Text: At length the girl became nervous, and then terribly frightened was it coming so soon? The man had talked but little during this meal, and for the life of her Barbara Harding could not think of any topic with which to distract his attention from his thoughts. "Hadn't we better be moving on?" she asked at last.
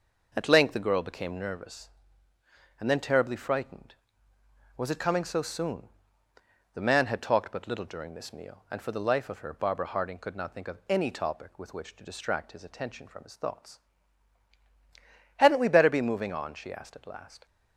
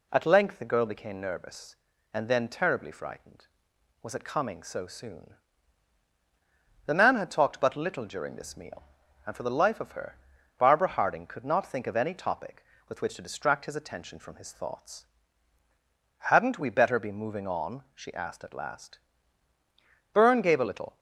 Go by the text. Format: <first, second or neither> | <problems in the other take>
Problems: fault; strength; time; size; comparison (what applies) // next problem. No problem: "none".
first | pauses between "her" and "Barbara"; at 10.1 s; 0.40 s long // goes on to say "Byrne gave a little"; noticeable; from 20.1 s on; 0.86 s long